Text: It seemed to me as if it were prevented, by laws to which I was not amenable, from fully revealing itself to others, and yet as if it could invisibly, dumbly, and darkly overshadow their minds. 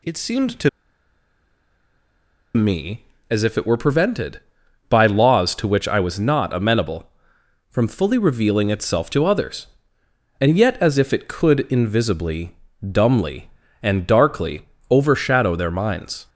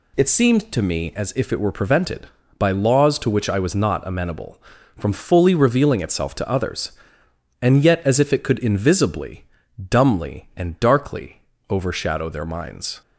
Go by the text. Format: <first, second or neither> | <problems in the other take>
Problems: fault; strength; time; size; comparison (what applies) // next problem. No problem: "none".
second | pauses between "to" and "me"; strong; at 0.6 s; 1.8 s long // pauses between "darkly" and "overshadow"; slight; at 14.6 s; 0.28 s long; slight in the second